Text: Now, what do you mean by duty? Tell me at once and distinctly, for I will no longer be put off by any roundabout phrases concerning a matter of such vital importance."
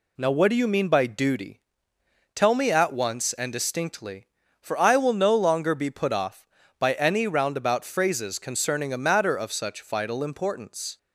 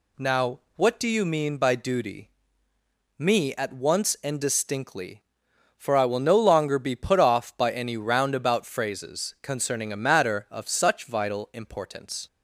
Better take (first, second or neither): first